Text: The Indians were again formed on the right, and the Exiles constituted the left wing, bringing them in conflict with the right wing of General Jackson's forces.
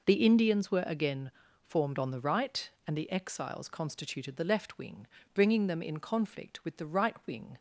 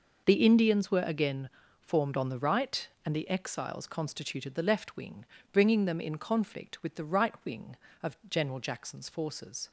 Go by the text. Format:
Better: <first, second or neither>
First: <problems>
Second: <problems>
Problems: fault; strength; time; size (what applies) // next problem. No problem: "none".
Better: second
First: pauses between "again" and "formed"; slight; at 1.3 s; 0.30 s long // stops before "of General Jackson's forces"; at 7.5 s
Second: pauses between "again" and "formed"; slight; at 1.4 s; 0.30 s long